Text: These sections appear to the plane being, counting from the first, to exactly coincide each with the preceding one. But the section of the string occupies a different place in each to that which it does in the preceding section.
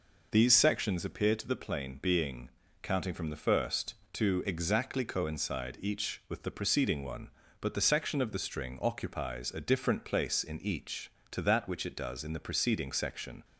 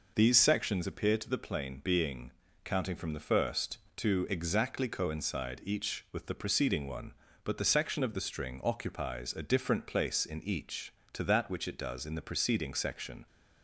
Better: neither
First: none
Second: none

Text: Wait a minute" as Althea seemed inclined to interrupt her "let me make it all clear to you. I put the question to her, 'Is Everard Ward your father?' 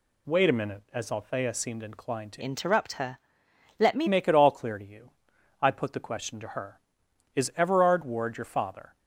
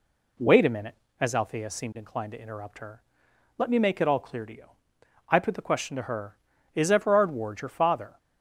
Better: second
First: changes voice from "interrupt" to "me"; from 2.4 to 4.0 s; 1.6 s long // pauses between "her" and "let"; noticeable; at 3.1 s; 0.58 s long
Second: pauses between "her" and "let"; noticeable; at 3.0 s; 0.56 s long

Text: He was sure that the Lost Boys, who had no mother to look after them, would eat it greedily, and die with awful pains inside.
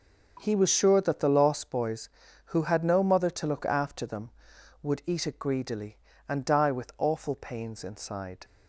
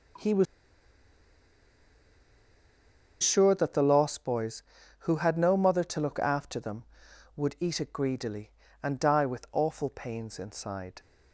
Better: first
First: starts louder than the rest; noticeable; until 1.4 s; 6 dB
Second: starts louder than the rest; until 3.9 s; 6.5 dB // pauses between "was" and "sure"; strong; at 0.4 s; 2.7 s long

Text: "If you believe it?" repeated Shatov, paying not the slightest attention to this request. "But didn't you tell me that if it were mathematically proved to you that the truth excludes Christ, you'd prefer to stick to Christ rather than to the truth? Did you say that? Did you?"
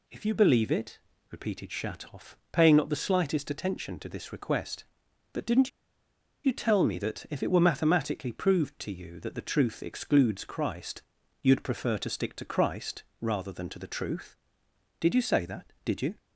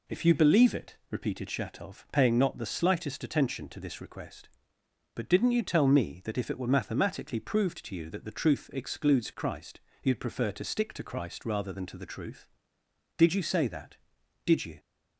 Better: second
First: pauses between "didn't" and "you"; noticeable; at 5.6 s; 0.74 s long // pauses between "Christ" and "rather"; slight; at 13.0 s; 0.18 s long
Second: none

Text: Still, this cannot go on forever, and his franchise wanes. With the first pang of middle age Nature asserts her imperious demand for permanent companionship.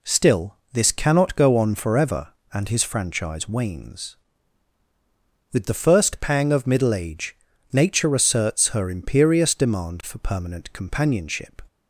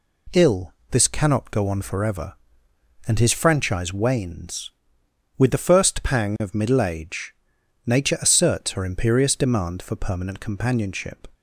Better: first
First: pauses between "age" and "Nature"; at 7.3 s; 0.38 s long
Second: says "Ill" for "Still"; at 0.3 s // pauses between "age" and "Nature"; noticeable; at 7.3 s; 0.52 s long

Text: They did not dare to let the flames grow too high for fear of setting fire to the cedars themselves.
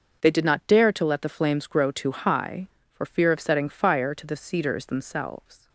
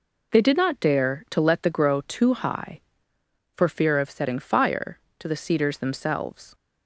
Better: first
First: none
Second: skips "flames"; at 1.7 s

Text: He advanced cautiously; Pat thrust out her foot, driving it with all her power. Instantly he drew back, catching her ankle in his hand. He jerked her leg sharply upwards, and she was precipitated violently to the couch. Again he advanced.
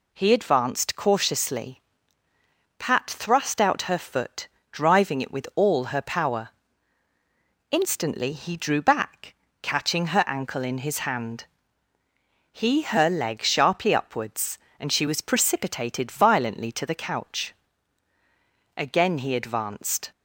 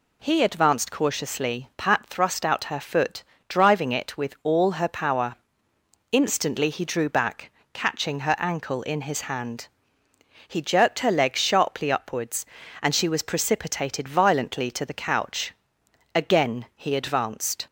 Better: second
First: skips "jerked"; at 12.8 s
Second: none

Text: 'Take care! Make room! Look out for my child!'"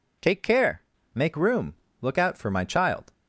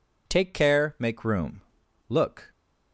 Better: first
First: none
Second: stops before "out for my child"; at 2.5 s

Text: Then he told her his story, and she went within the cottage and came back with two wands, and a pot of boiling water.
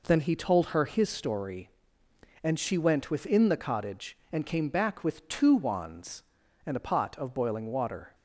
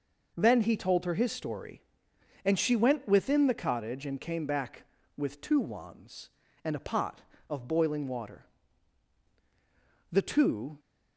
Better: first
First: none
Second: goes on to say "The two"; noticeable; from 10.1 s on; 0.68 s long

